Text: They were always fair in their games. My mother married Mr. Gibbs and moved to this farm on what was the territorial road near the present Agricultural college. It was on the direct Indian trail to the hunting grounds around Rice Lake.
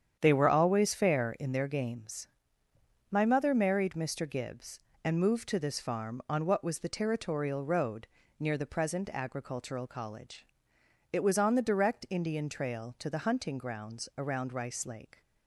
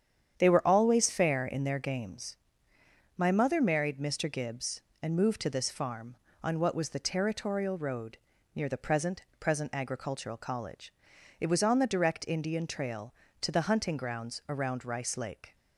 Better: first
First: starts louder than the rest; strong; until 1.2 s; 8.5 dB // pauses between "road" and "near"; slight; at 8.0 s; 0.32 s long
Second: starts louder than the rest; strong; until 1.4 s; 8.5 dB // pauses between "road" and "near"; slight; at 8.1 s; 0.36 s long // says "present" twice; at 9.3 s

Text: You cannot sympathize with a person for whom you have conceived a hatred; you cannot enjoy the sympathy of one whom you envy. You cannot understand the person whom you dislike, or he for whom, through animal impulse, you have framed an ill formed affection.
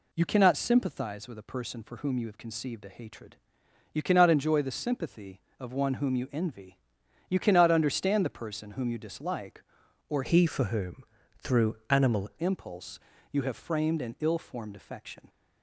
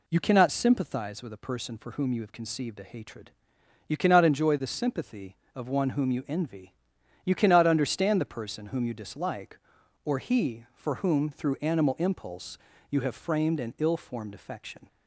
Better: second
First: changes voice from "he" to "animal"; from 10.2 to 12.3 s; 2.1 s long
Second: none

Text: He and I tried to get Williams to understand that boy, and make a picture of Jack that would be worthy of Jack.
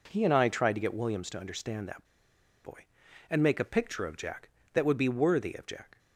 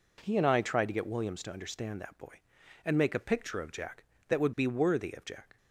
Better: second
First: pauses between "that" and "boy"; noticeable; at 2.0 s; 0.59 s long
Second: none

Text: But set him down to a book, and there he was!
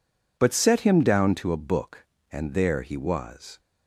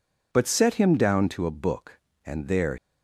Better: first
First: none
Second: stops before "he was"; at 2.7 s

